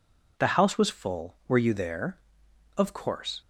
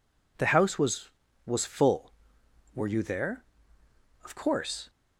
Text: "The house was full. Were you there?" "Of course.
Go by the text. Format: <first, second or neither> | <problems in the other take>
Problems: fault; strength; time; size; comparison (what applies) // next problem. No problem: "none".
first | says "was" twice; at 1.4 s